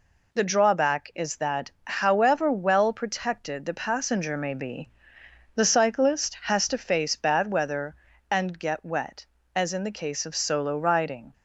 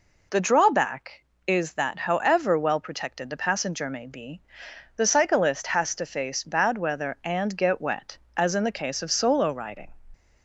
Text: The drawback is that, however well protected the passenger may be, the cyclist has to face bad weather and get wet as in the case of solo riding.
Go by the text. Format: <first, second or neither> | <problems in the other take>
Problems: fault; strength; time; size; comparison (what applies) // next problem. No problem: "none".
neither | none